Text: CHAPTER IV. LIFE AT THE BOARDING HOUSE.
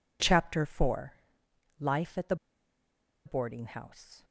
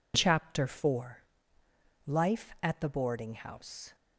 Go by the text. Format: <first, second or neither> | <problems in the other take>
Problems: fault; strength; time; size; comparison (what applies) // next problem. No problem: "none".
second | pauses between "THE" and "BOARDING"; noticeable; at 2.3 s; 0.90 s long